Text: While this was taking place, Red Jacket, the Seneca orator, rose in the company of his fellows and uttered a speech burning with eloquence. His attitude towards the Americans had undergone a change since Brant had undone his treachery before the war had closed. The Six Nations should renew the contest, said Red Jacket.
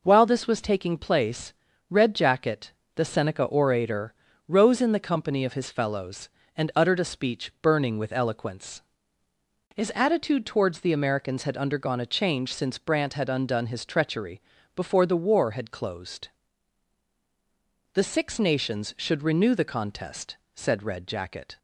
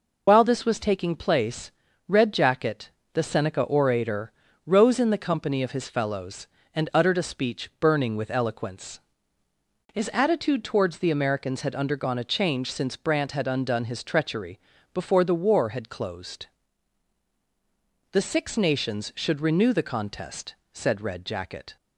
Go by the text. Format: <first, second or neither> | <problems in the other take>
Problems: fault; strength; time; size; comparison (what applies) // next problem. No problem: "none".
first | loses the start of "While"; at 0.2 s; 55 ms // pauses between "treachery" and "before"; slight; at 14.6 s; 0.32 s long; slight in the first